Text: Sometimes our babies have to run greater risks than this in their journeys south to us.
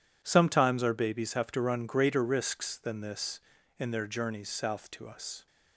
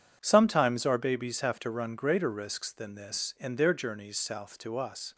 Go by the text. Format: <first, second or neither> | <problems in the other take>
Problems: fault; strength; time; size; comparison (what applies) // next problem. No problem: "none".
neither | none